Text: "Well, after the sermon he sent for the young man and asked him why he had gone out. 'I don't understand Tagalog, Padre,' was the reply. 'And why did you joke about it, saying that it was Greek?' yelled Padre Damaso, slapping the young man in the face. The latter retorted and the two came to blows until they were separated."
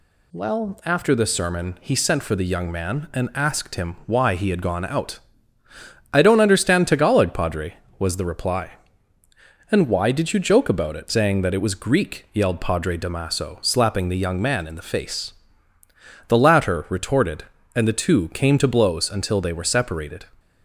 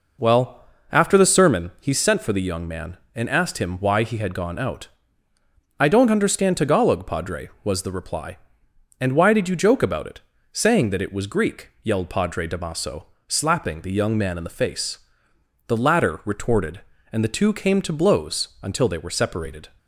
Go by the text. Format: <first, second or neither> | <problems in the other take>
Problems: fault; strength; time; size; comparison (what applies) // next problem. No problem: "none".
first | starts louder than the rest; noticeable; until 1.6 s; 4.5 dB